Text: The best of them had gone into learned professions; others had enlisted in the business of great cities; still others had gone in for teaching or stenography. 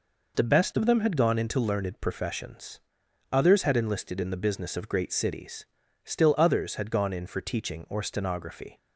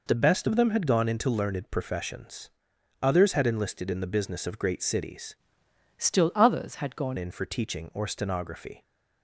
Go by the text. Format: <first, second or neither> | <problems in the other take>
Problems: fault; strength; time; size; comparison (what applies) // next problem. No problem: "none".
first | changes voice from "still" to "gone"; from 5.9 to 7.1 s; 1.2 s long